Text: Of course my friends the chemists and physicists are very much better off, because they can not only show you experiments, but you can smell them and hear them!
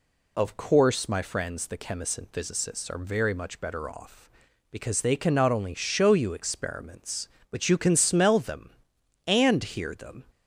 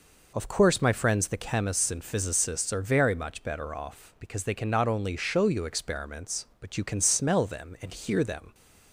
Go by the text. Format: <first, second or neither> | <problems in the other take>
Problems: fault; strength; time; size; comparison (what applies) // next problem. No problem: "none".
neither | none